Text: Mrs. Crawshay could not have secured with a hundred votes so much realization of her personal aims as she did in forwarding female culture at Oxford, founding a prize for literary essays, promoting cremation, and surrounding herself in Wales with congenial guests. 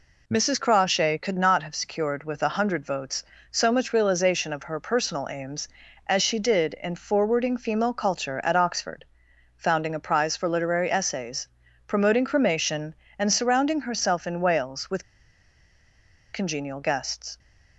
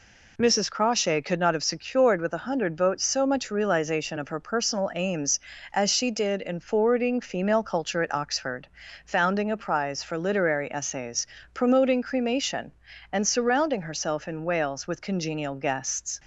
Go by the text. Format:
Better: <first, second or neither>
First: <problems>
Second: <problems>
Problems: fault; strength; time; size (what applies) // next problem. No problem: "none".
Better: second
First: pauses between "with" and "congenial"; strong; at 15.0 s; 1.2 s long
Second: none